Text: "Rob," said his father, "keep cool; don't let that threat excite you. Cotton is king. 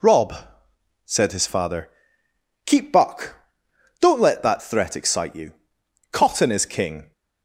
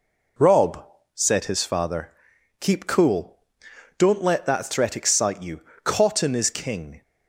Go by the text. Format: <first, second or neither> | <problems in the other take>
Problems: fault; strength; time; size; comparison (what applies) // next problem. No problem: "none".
second | says "buck" for "cool"; at 2.9 s